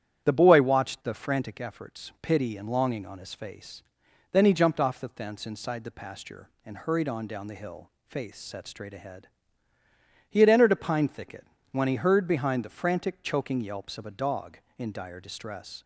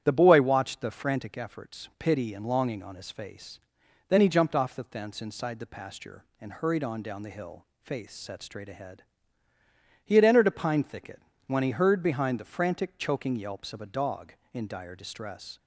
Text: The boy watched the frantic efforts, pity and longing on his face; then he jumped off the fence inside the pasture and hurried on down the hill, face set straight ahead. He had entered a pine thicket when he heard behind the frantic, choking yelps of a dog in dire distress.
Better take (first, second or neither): neither